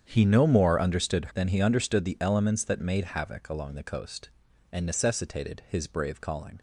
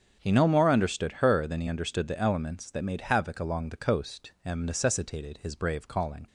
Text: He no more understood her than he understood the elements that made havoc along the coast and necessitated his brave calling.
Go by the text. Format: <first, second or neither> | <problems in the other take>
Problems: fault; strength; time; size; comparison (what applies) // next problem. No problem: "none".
second | starts louder than the rest; strong; until 1.0 s; 8 dB; strong in the second // skips "her"; at 1.3 s